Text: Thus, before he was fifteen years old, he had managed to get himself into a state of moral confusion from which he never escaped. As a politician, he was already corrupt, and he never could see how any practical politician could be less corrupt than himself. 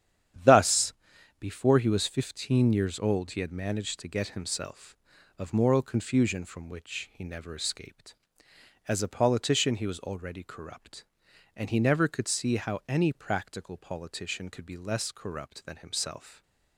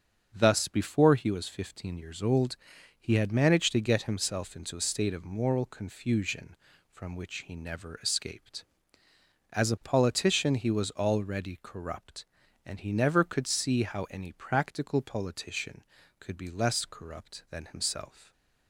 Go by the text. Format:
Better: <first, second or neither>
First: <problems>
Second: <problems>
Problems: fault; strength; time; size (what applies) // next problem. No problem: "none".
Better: second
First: starts louder than the rest; strong; until 1.8 s; 9.5 dB // skips "into a state"; at 5.1 s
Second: starts louder than the rest; strong; until 1.3 s; 7 dB